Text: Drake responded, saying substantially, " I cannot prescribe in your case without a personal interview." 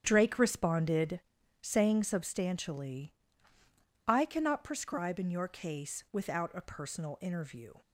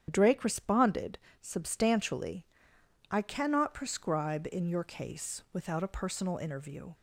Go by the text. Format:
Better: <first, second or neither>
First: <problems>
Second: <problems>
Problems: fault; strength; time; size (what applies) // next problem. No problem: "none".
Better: first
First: starts louder than the rest; noticeable; until 1.0 s; 6 dB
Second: starts louder than the rest; strong; until 1.1 s; 9 dB // skips "saying"; at 1.3 s